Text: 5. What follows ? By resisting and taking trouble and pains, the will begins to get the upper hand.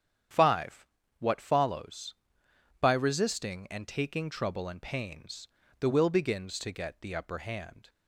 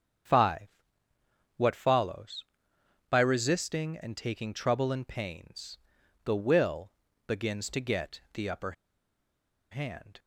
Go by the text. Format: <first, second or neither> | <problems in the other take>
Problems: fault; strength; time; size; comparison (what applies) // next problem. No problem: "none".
first | starts louder than the rest; strong; until 2.1 s; 8.5 dB; strong in the first // pauses between "will" and "begins"; at 6.9 s; 0.38 s long // pauses between "upper" and "hand"; at 8.7 s; 0.98 s long